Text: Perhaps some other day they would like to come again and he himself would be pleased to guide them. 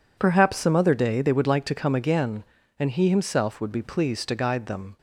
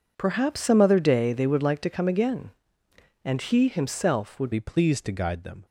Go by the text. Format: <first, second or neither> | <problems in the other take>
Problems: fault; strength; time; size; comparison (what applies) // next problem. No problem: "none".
first | changes voice at "be"; from 4.5 s on; 1.1 s long